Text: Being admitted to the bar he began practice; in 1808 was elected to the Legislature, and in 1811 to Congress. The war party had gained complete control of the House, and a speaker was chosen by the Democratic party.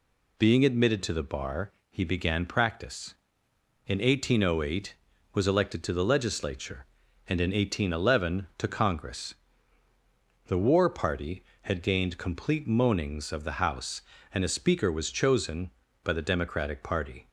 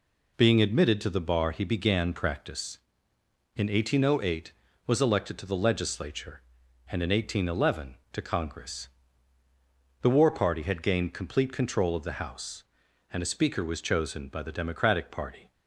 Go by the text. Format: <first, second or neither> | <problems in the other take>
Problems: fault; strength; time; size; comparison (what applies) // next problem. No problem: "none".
second | pauses between "bar" and "he"; slight; at 1.7 s; 0.22 s long // says "moanings" for "control"; at 12.6 s